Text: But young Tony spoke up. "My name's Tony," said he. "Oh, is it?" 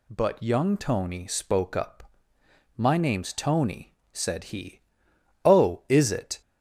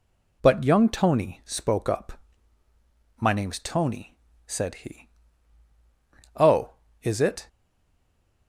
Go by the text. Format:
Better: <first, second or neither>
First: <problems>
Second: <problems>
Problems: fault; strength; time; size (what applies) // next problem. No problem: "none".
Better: first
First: none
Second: stays silent after the last word; from 7.4 s on; 1.0 s long